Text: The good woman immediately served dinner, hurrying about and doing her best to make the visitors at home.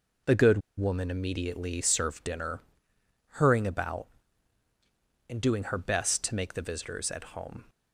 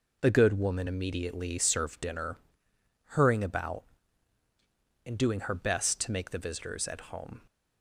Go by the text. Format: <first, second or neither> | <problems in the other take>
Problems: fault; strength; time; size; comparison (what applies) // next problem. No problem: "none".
second | pauses between "good" and "woman"; slight; at 0.6 s; 0.17 s long